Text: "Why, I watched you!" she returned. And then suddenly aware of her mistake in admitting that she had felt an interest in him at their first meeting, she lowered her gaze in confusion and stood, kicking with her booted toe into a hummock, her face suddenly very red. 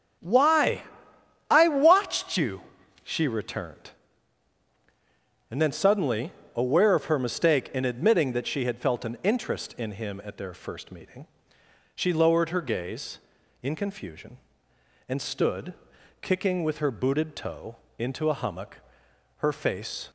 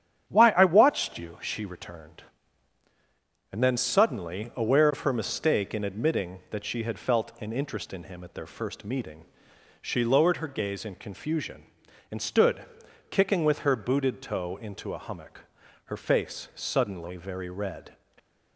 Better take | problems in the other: second | starts louder than the rest; strong; until 1.8 s; 8.5 dB; strong in the second // pauses between "suddenly" and "aware"; slight; at 6.3 s; 0.24 s long // pauses between "toe" and "into"; slight; at 17.7 s; 0.24 s long // stops before "suddenly very red"; at 20.0 s

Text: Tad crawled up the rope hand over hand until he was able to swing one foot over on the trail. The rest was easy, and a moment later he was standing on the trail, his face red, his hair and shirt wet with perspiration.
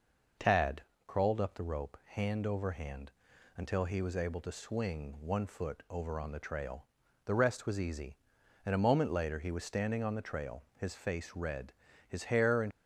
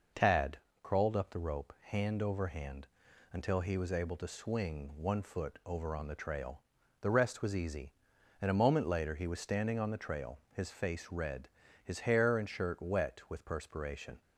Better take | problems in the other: second | pauses between "Tad" and "crawled"; slight; at 0.8 s; 0.24 s long; slight in the second // pauses between "hand" and "until"; noticeable; at 3.1 s; 0.46 s long; noticeable in the second // stops before "shirt wet with perspiration"; at 12.7 s

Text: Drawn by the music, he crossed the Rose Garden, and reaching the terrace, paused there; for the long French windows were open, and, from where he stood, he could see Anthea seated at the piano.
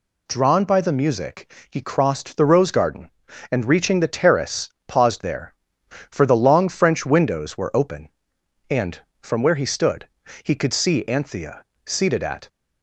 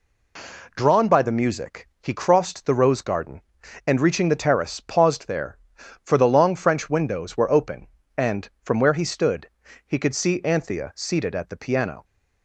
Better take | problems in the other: second | pauses between "Anthea" and "seated"; slight; at 11.6 s; 0.20 s long // stops before "the piano"; at 12.4 s

